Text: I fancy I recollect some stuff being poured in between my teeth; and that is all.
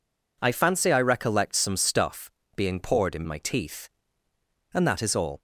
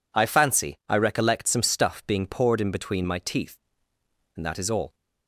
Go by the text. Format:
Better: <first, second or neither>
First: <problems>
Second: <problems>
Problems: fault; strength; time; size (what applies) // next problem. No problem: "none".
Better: second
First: pauses between "stuff" and "being"; slight; at 2.2 s; 0.24 s long // skips "between"; at 3.2 s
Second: none